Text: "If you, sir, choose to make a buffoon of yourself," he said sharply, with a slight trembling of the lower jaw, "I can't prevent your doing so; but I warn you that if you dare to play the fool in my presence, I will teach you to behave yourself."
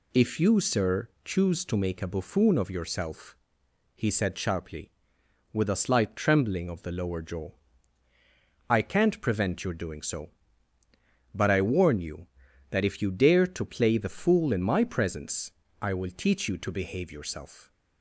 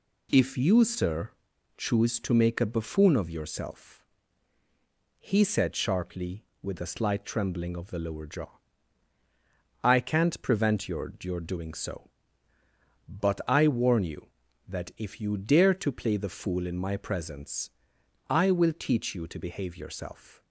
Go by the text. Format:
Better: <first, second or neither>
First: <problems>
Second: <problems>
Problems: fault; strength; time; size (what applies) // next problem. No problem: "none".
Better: first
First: none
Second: says "your" twice; at 11.2 s